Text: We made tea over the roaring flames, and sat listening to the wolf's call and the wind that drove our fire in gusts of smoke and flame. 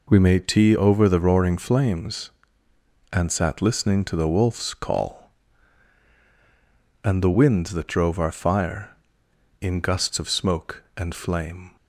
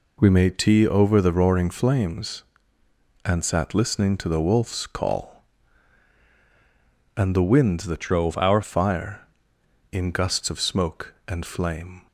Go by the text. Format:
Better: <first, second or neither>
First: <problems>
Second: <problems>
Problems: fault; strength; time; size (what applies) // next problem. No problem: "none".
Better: first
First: none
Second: changes voice from "drove" to "our"; from 8.0 to 8.6 s; 0.6 s long